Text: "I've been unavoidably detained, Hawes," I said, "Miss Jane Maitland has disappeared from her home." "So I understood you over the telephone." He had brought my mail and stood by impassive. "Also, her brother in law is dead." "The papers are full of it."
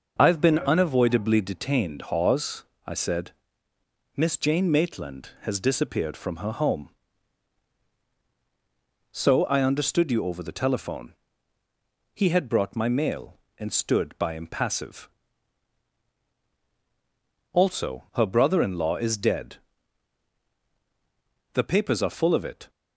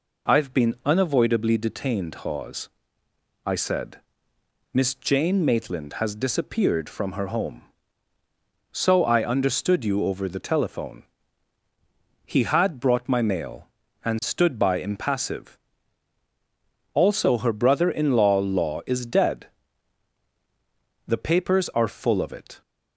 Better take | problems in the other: first | says "law" twice; at 18.3 s

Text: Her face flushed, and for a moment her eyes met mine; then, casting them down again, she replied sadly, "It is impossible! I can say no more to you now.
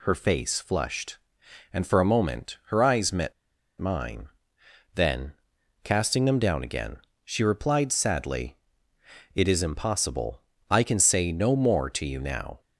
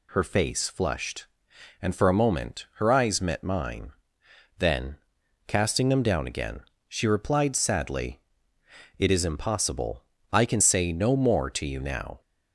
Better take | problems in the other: second | pauses between "met" and "mine"; noticeable; at 3.3 s; 0.47 s long

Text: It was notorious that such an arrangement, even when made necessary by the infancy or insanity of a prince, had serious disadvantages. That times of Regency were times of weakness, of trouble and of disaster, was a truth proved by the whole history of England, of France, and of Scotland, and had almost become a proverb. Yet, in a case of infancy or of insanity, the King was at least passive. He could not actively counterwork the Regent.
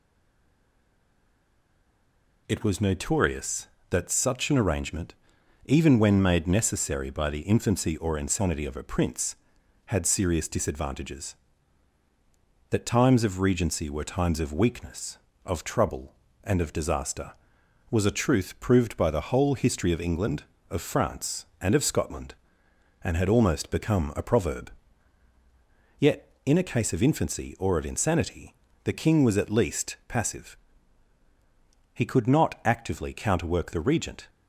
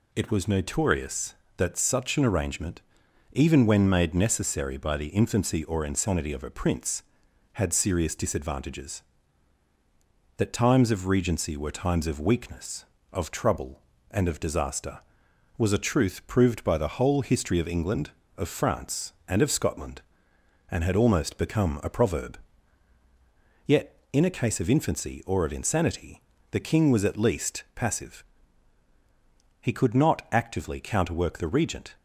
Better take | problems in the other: second | stays silent before the first word; until 2.4 s; 2.4 s long

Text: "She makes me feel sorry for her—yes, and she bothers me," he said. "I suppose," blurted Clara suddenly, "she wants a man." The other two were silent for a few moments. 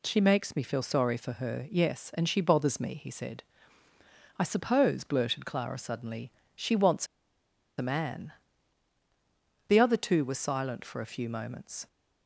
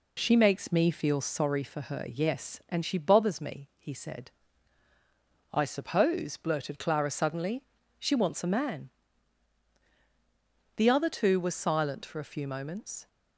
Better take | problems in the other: second | pauses between "wants" and "a"; noticeable; at 7.0 s; 0.72 s long

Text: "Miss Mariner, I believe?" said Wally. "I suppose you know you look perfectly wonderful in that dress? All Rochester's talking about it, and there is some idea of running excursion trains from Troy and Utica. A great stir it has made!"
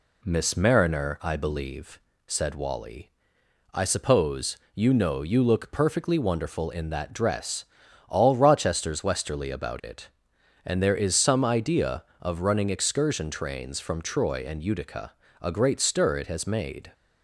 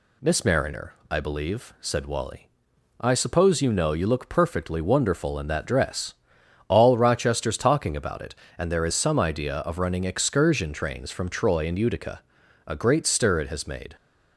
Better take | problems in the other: second | pauses between "suppose" and "you"; slight; at 4.5 s; 0.20 s long // says "westerly" for "talking"; at 9.0 s

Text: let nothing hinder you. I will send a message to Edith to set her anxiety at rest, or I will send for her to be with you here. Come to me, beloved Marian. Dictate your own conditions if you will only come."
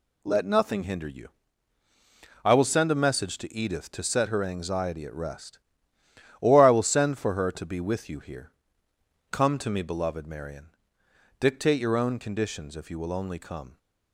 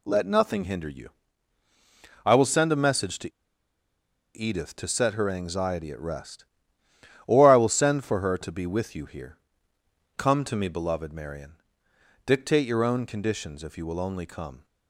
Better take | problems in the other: first | pauses between "to" and "Edith"; at 3.3 s; 1.0 s long

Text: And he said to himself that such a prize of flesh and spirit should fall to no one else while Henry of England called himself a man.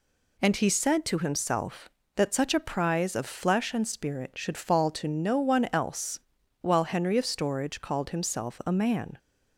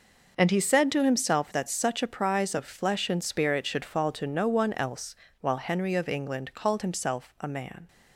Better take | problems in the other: second | pauses between "else" and "while"; at 6.2 s; 0.40 s long; slight in the second // says "Storage" for "England"; at 7.2 s

